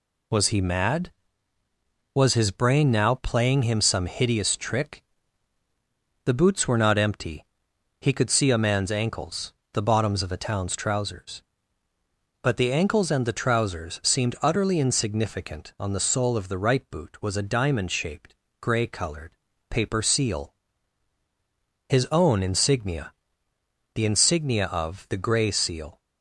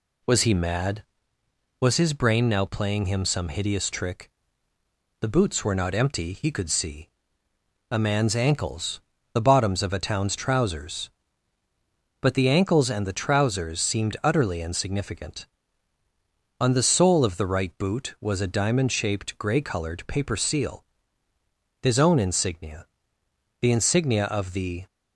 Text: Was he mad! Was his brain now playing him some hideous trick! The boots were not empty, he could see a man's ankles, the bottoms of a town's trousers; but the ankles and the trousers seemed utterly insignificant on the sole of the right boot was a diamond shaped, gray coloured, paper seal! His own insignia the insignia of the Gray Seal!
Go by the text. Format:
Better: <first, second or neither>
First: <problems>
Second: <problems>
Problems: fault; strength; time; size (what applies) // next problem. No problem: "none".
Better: first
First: pauses between "insignia" and "the"; noticeable; at 23.1 s; 0.82 s long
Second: pauses between "see" and "a"; noticeable; at 7.0 s; 0.82 s long // pauses between "insignia" and "the"; noticeable; at 22.8 s; 0.74 s long // stops before "Gray Seal"; at 24.8 s